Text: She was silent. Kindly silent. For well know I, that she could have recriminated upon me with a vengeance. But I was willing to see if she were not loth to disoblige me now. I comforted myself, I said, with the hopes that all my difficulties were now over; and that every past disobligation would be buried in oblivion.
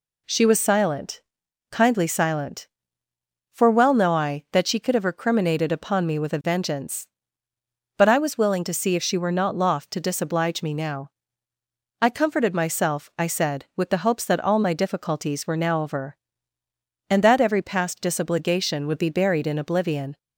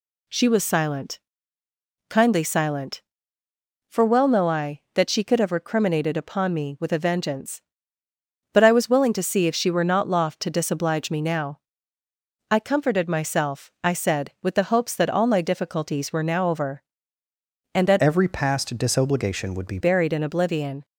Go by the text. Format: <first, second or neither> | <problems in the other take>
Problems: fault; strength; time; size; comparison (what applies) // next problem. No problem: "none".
first | changes voice from "every" to "be"; from 18.0 to 19.7 s; 1.7 s long